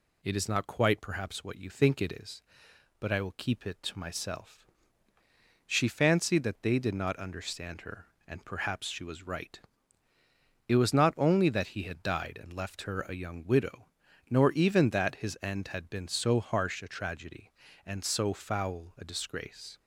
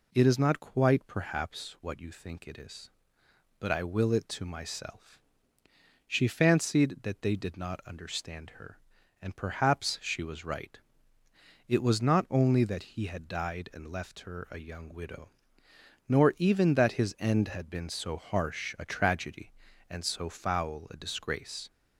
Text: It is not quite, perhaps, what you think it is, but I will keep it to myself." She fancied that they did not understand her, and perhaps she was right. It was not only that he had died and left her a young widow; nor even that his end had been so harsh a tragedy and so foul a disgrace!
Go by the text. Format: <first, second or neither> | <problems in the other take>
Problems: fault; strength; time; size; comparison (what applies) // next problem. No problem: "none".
first | skips "keep"; at 4.1 s